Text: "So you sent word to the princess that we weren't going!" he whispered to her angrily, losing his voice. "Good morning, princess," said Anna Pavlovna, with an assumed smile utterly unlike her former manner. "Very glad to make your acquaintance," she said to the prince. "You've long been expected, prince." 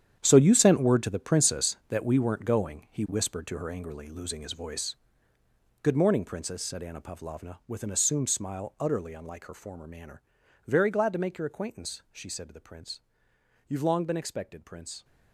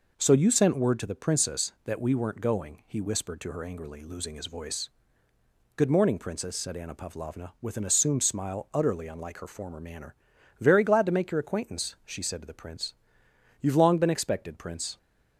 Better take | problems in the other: second | gets quieter; strong; throughout; 12.5 dB

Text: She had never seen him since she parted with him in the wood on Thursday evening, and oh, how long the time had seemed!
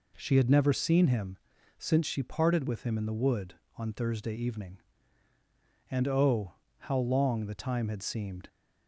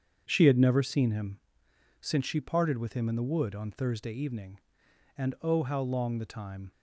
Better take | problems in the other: first | starts louder than the rest; strong; until 1.2 s; 7.5 dB // pauses between "him" and "since"; noticeable; at 1.3 s; 0.62 s long; also in the first // stops before "had seemed"; at 6.7 s

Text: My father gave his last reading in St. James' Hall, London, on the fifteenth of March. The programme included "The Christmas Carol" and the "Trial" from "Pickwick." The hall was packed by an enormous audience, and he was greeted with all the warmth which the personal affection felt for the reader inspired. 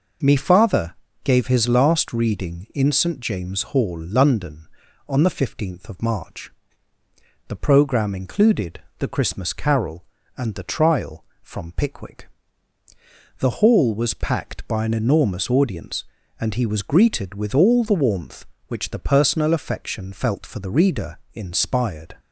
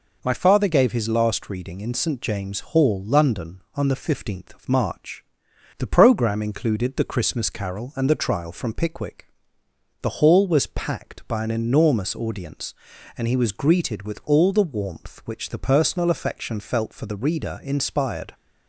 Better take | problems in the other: second | says "Me" for "My"; at 0.2 s // pauses between "father" and "gave"; slight; at 0.9 s; 0.30 s long // pauses between "included" and "The"; slight; at 8.8 s; 0.18 s long // pauses between "reader" and "inspired"; slight; at 21.1 s; 0.16 s long

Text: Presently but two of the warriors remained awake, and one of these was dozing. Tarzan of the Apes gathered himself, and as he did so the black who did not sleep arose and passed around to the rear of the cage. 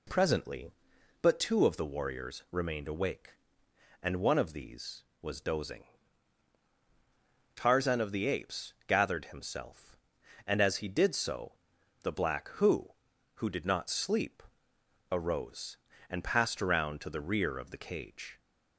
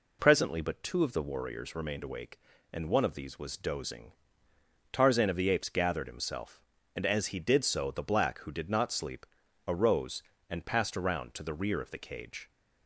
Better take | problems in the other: second | pauses between "so" and "the"; noticeable; at 11.5 s; 0.48 s long // says "who" twice; at 13.3 s // pauses between "sleep" and "arose"; noticeable; at 14.4 s; 0.70 s long; also in the second

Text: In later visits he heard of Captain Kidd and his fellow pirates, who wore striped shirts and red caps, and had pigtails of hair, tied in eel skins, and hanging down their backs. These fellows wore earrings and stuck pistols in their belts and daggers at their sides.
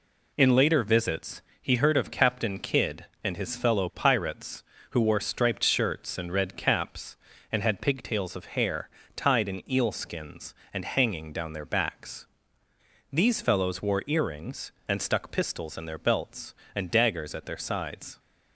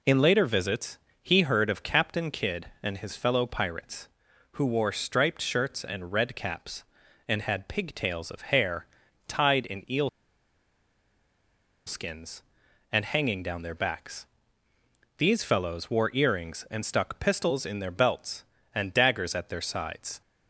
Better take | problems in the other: first | pauses between "visits" and "he"; slight; at 0.9 s; 0.24 s long; slight in the first // pauses between "eel" and "skins"; strong; at 10.0 s; 1.7 s long

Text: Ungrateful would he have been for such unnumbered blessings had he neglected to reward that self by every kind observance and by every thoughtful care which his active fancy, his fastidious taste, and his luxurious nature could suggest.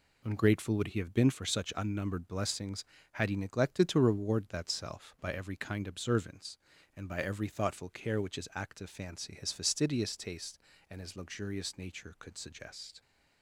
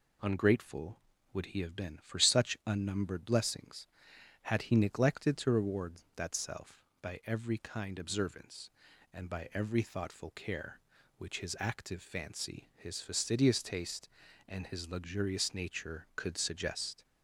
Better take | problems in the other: neither | none

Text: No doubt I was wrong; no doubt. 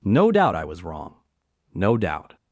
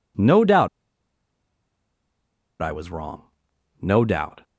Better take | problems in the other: first | pauses between "doubt" and "I"; strong; at 0.6 s; 1.9 s long

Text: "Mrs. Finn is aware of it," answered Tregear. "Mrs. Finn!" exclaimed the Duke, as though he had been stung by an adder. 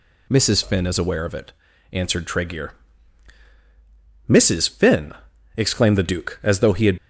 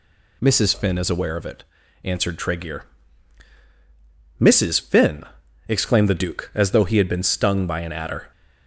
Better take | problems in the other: second | stops before "been stung by an adder"; at 6.9 s

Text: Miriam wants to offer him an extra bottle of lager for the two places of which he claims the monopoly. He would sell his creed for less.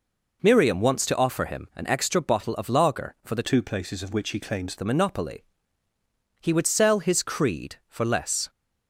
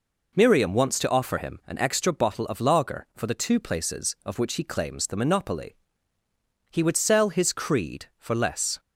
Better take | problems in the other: second | changes voice from "two" to "claims"; from 3.4 to 4.7 s; 1.3 s long

